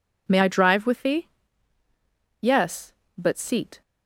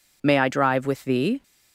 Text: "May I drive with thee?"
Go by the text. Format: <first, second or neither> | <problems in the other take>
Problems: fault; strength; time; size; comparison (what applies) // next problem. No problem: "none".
second | goes on to say "Yes but seat"; from 2.4 s on; 1.4 s long